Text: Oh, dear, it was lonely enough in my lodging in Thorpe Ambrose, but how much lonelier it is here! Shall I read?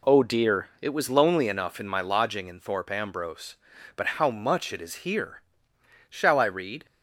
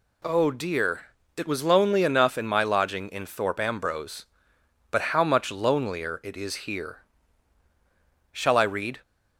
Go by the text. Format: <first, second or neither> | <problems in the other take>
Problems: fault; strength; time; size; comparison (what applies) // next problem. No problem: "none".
second | skips "lonelier"; at 4.7 s